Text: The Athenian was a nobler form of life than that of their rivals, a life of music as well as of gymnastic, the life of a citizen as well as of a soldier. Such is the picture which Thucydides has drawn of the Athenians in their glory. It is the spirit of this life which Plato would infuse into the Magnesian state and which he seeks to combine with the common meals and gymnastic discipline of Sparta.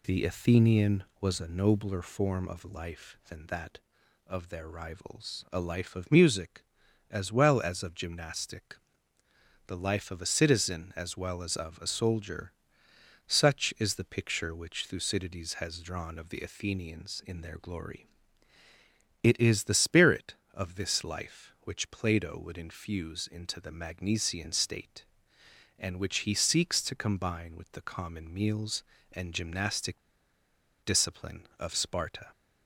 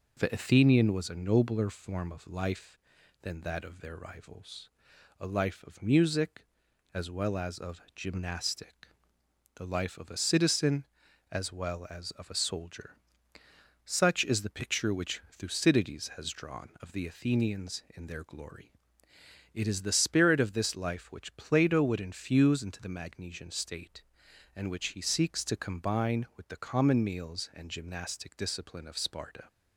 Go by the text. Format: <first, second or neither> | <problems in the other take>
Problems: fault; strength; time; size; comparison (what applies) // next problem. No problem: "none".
second | pauses between "gymnastic" and "discipline"; noticeable; at 29.9 s; 0.90 s long